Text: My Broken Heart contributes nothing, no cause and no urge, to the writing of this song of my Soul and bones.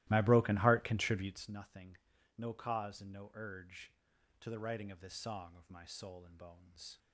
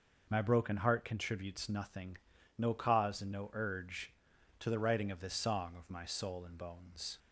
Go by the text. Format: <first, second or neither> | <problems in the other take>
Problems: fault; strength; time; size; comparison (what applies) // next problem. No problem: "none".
second | starts louder than the rest; strong; until 1.4 s; 17 dB